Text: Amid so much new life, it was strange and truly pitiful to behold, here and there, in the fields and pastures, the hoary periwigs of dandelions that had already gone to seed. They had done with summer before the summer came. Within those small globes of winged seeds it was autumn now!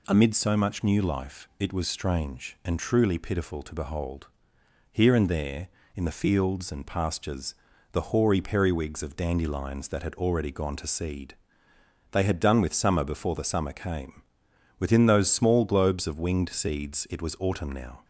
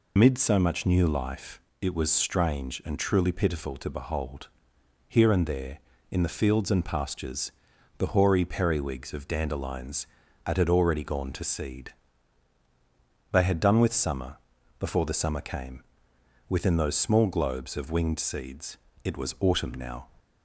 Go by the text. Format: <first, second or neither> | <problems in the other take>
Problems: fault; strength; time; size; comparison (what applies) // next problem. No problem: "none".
first | loses the start of "Amid"; at 0.1 s; 95 ms // pauses between "summer" and "before"; at 14.3 s; 0.42 s long // pauses between "seeds" and "it"; slight; at 18.7 s; 0.28 s long